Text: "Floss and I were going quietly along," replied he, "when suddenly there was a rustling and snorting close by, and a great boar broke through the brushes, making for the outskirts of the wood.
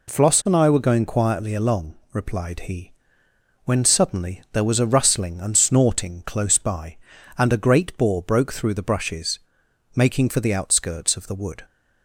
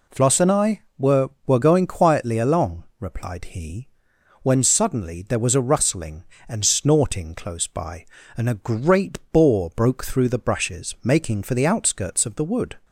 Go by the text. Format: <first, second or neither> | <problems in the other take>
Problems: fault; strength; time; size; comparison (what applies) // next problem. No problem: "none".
first | says "were" twice; at 1.4 s